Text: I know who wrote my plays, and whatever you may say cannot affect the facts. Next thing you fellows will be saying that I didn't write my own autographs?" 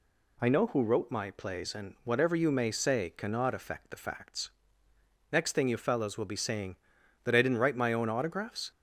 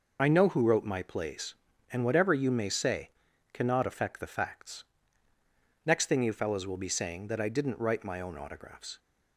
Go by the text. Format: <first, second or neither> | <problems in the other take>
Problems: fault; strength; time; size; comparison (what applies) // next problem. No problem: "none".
first | loses the start of "I"; at 0.1 s; 55 ms // pauses between "say" and "cannot"; noticeable; at 3.0 s; 0.46 s long